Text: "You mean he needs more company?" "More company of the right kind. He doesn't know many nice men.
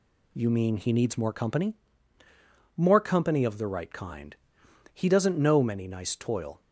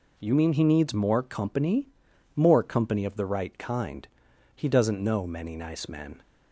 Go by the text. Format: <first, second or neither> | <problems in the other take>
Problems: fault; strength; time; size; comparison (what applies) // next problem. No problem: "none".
second | says "toil" for "men"; at 6.1 s